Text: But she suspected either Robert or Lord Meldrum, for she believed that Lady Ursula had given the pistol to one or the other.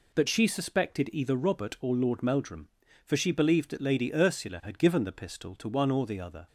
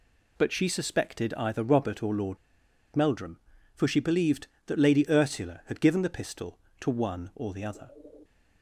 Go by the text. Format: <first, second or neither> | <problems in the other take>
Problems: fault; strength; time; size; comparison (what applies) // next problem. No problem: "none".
first | pauses between "Lord" and "Meldrum"; noticeable; at 2.3 s; 0.58 s long